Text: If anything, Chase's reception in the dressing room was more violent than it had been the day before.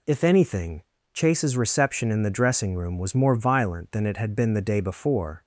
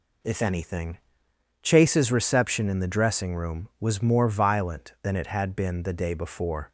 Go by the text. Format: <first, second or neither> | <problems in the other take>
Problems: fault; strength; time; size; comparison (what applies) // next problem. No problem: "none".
neither | none